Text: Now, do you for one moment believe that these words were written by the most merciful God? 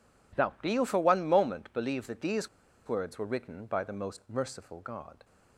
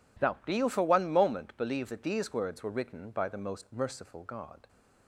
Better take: second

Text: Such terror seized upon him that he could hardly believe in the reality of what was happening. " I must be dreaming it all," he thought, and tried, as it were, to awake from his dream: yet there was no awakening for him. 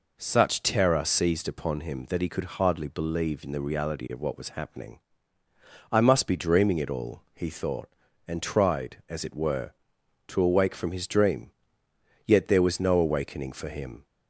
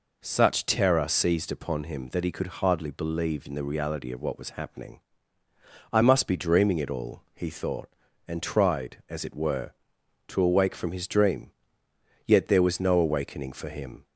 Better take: neither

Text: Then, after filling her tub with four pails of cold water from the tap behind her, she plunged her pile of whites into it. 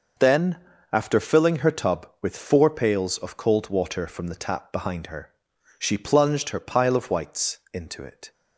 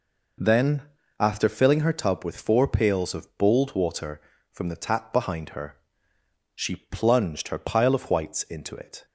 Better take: first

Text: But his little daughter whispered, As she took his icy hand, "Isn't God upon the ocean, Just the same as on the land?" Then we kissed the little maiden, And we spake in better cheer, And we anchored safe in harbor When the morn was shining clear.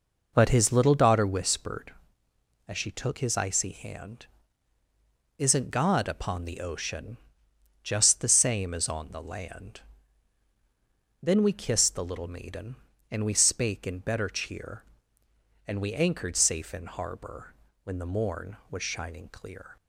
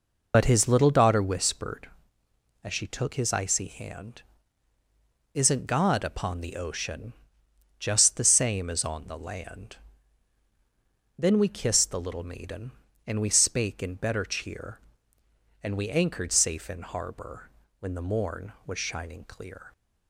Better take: first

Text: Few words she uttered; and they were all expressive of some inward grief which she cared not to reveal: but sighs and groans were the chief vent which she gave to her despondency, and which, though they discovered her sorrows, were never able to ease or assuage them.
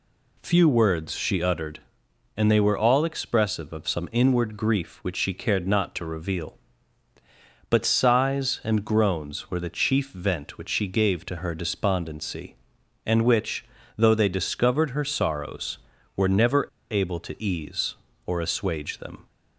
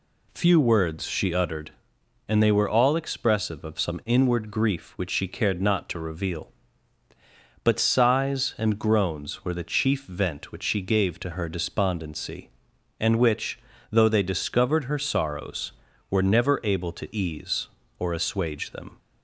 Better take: second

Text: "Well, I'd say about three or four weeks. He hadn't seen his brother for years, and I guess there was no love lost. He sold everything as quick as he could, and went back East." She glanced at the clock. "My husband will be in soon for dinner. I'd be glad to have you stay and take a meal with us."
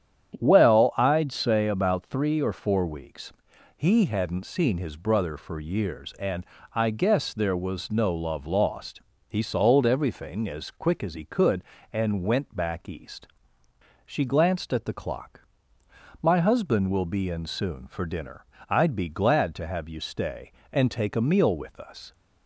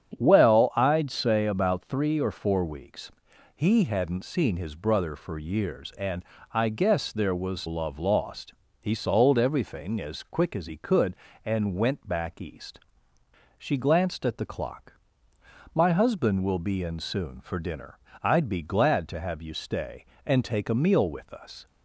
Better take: first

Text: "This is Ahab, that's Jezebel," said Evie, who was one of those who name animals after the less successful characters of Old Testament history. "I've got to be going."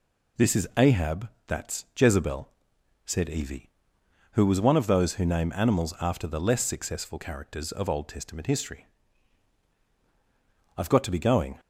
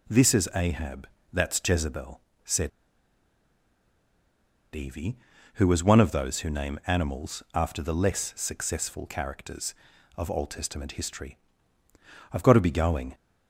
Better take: first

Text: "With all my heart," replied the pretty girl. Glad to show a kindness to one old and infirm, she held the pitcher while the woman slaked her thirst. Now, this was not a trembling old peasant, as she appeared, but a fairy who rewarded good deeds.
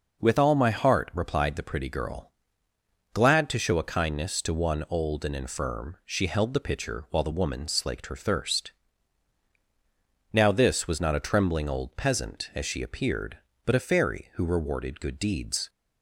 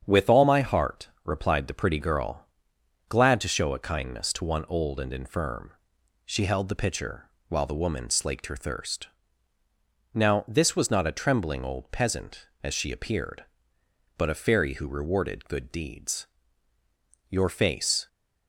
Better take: first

